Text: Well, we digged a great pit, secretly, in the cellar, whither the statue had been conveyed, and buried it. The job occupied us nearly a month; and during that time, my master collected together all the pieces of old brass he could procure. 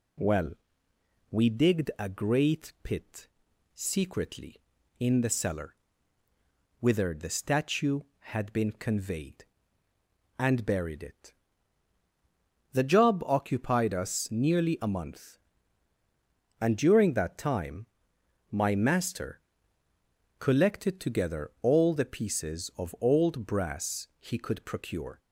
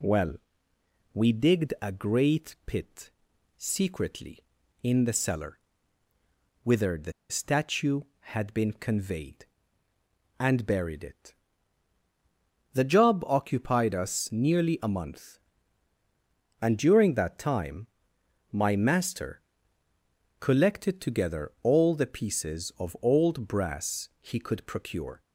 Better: first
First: pauses between "master" and "collected"; at 19.4 s; 1.0 s long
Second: pauses between "the" and "statue"; slight; at 7.1 s; 0.18 s long // pauses between "master" and "collected"; at 19.4 s; 1.0 s long

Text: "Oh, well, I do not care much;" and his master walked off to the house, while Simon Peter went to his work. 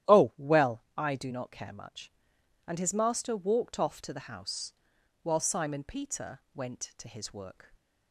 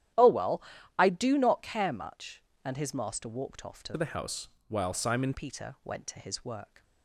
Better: first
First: starts louder than the rest; strong; until 1.2 s; 12 dB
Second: starts louder than the rest; strong; until 1.5 s; 11.5 dB // changes voice from "the" to "Simon"; from 3.9 to 5.3 s; 1.4 s long

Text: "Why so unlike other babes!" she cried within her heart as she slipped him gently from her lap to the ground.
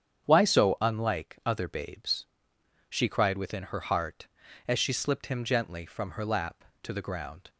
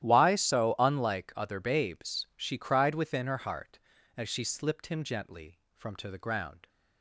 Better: first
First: starts louder than the rest; strong; until 1.2 s; 8.5 dB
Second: starts louder than the rest; strong; until 1.0 s; 12.5 dB // skips "her lap"; at 5.9 s

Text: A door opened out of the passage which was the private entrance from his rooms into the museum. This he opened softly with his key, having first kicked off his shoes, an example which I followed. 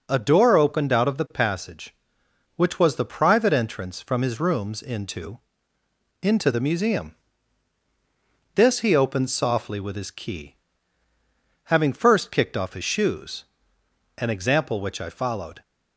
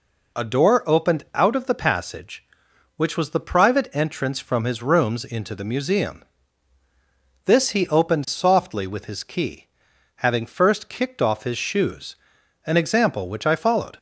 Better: second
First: says "into" twice; at 6.2 s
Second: none

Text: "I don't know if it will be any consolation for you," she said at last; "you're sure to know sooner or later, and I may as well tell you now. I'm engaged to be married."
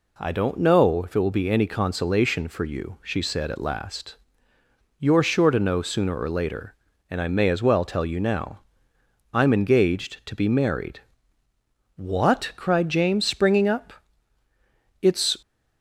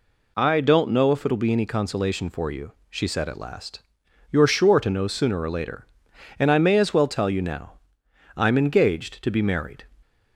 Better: second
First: goes on to say "What cried James springing up It's"; strong; from 11.9 s on; 3.4 s long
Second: none

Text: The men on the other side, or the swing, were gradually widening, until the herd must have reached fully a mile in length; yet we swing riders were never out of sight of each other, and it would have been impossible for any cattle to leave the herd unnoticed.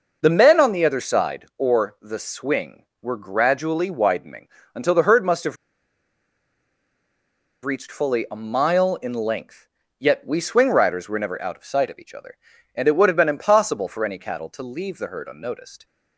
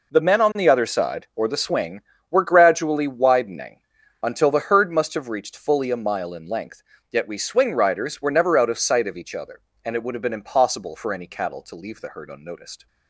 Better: second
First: pauses between "have" and "reached"; strong; at 5.5 s; 2.0 s long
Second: none

